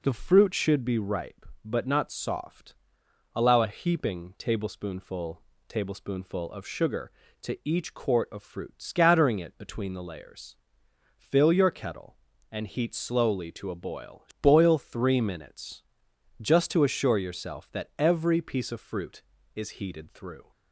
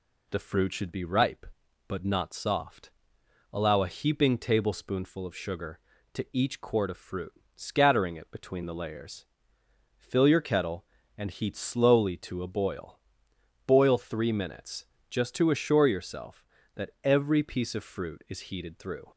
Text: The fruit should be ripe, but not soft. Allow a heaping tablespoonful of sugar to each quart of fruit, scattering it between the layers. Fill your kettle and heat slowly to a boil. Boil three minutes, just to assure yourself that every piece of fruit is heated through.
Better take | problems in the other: second | says "tablespoonful" twice; at 5.6 s

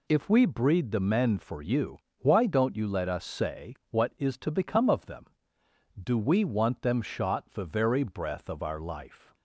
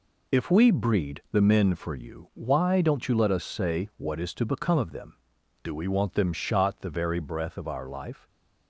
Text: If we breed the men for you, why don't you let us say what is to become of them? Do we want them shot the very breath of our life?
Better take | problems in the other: neither | none

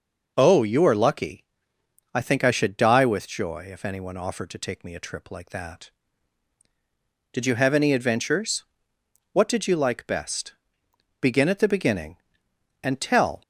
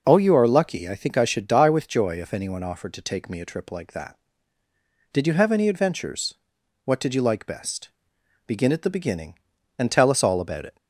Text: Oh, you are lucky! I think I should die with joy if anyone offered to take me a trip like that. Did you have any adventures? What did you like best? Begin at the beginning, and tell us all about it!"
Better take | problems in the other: second | stops before "us all about it"; at 13.4 s

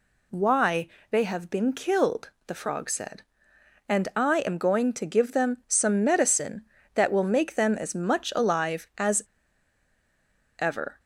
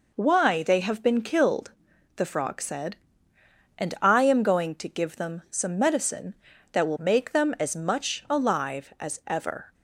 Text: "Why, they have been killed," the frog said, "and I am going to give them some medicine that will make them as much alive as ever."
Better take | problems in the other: second | pauses between "as" and "ever"; strong; at 9.2 s; 1.3 s long

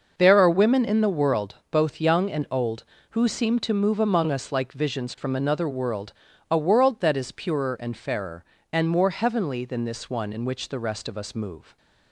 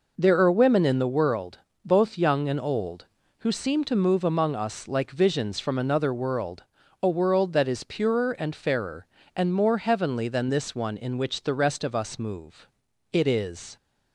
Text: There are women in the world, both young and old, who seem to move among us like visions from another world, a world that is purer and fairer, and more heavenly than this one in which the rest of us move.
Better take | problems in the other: first | goes on to say "It is"; noticeable; from 13.1 s on; 0.64 s long

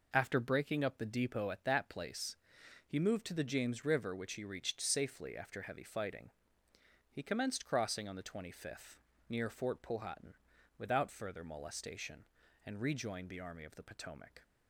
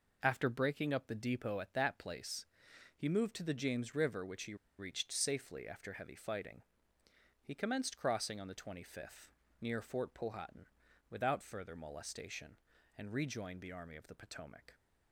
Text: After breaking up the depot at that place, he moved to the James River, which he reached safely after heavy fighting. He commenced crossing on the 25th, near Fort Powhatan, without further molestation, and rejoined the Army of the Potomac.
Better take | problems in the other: first | pauses between "he" and "reached"; slight; at 4.5 s; 0.25 s long

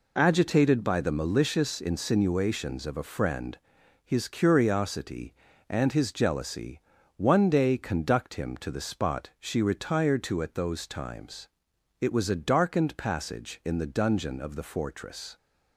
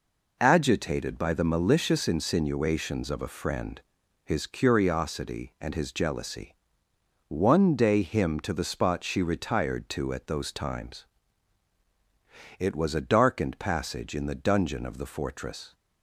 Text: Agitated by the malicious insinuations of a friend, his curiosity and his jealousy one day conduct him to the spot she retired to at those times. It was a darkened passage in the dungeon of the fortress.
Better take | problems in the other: first | pauses between "jealousy" and "one"; noticeable; at 6.5 s; 0.74 s long; slight in the first // skips "conduct"; at 7.9 s

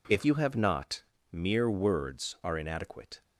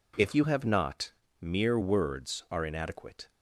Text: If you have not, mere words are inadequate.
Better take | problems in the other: neither | none

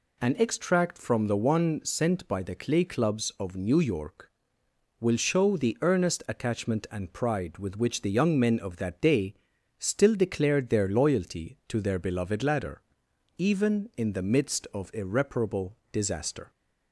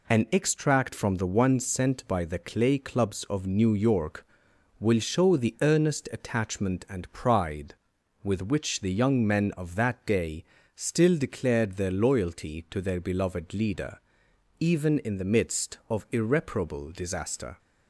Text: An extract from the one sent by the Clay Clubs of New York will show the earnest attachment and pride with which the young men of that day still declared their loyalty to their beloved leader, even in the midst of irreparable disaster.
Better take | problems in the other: second | pauses between "day" and "still"; at 9.3 s; 0.44 s long; slight in the second // says "ladder" for "leader"; at 12.4 s // pauses between "irreparable" and "disaster"; slight; at 15.7 s; 0.16 s long

